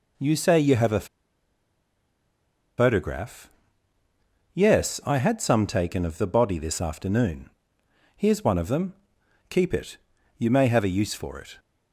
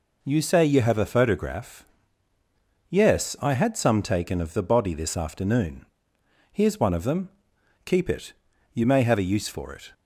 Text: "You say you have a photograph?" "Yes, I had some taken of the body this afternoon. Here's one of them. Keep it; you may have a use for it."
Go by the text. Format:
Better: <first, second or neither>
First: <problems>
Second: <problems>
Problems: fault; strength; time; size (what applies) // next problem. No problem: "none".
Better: second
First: pauses between "a" and "photograph"; strong; at 1.0 s; 1.7 s long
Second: none